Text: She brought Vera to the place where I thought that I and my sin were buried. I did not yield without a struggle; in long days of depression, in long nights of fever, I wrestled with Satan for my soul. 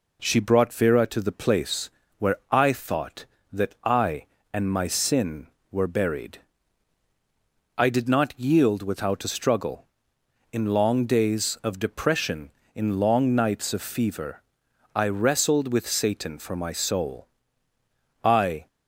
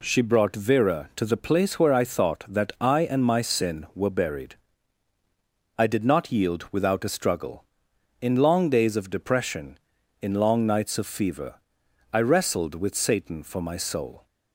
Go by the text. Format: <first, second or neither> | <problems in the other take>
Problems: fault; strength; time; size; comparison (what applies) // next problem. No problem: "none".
second | pauses between "place" and "where"; slight; at 1.8 s; 0.30 s long // goes on to say "I"; slight; from 18.2 s on; 0.44 s long